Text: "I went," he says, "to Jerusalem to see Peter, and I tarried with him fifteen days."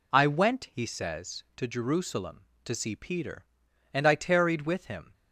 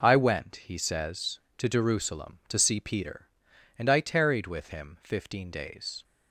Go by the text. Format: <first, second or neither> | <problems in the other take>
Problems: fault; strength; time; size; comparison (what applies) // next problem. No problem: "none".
second | stops before "fifteen days"; at 5.1 s